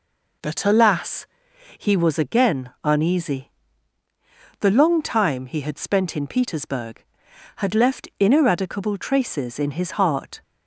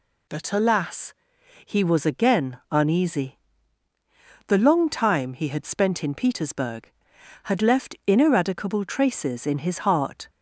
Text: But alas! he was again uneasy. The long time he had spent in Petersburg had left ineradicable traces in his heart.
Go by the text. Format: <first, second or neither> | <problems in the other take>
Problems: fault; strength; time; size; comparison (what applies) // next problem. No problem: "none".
second | starts louder than the rest; noticeable; until 2.0 s; 4.5 dB